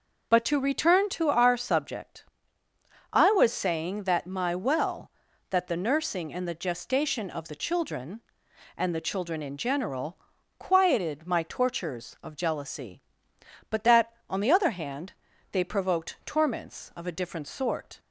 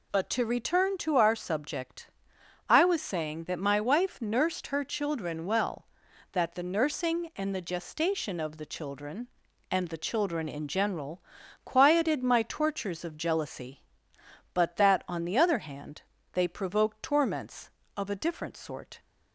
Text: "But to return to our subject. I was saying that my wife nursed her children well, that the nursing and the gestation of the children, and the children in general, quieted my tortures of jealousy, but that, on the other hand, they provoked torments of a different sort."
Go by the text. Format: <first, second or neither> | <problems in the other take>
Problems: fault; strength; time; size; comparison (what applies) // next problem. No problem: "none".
second | skips "wife nursed her children"; at 4.5 s